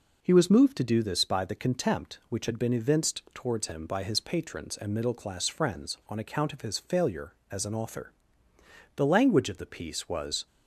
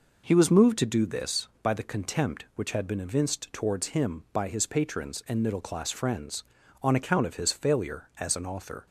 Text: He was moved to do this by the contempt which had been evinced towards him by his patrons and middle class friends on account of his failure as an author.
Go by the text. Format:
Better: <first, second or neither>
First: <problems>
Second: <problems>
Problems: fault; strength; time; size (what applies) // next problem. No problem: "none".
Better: second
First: goes on to say "The language of the piece was"; from 8.9 s on; 1.5 s long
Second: none